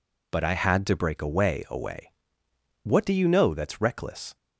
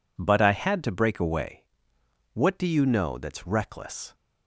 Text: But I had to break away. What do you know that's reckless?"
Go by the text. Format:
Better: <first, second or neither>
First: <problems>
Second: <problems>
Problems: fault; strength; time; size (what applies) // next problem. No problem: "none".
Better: second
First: says "away" twice; at 1.6 s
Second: none